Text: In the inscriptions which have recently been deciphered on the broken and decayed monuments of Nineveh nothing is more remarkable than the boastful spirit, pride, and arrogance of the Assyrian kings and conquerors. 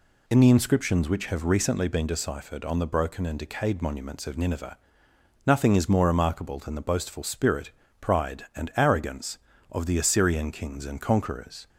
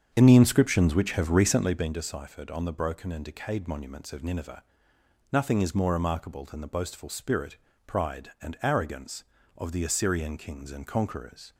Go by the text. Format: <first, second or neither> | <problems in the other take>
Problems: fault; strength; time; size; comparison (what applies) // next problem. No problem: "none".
first | starts louder than the rest; strong; until 1.9 s; 8 dB // pauses between "Nineveh" and "nothing"; noticeable; at 4.6 s; 0.70 s long; noticeable in the first